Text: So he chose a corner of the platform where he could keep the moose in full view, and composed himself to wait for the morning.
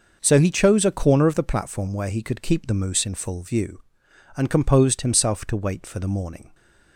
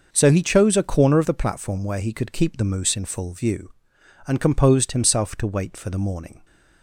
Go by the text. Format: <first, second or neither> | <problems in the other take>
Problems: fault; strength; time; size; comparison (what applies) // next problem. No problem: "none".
neither | none